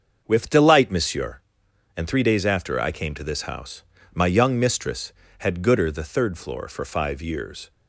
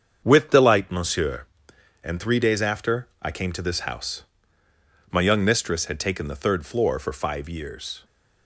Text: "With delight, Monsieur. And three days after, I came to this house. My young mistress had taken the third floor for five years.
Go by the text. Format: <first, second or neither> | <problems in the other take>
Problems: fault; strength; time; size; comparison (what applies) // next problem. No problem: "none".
second | starts louder than the rest; until 1.2 s; 6.5 dB; strong in the second // says "gooder" for "taken"; at 5.6 s